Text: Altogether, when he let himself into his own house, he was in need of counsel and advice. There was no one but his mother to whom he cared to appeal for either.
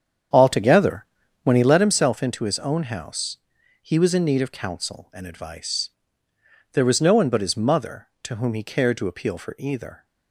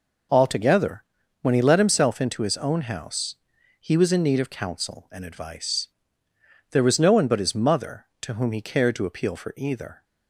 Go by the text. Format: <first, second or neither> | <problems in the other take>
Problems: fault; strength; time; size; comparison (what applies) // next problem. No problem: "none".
second | starts louder than the rest; strong; until 1.8 s; 8 dB